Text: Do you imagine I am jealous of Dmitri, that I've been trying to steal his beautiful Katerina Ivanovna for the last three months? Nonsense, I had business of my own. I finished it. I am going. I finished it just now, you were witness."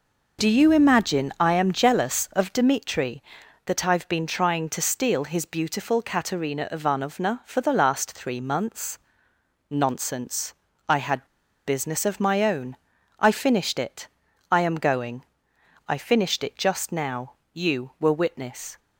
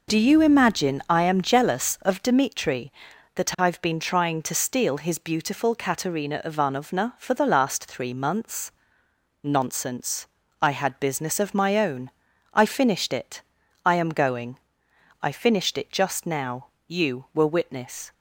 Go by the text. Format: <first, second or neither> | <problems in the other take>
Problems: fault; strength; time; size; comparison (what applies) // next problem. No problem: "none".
second | pauses between "had" and "business"; at 11.2 s; 0.40 s long